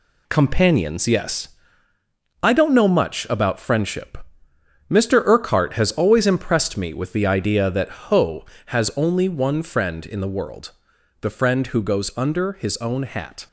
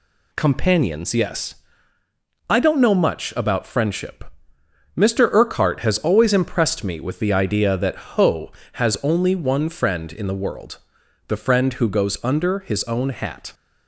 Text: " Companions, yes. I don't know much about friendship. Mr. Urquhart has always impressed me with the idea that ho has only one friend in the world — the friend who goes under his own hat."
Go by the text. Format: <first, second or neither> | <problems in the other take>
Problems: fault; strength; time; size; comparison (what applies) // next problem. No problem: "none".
second | gets quieter; throughout; 6.5 dB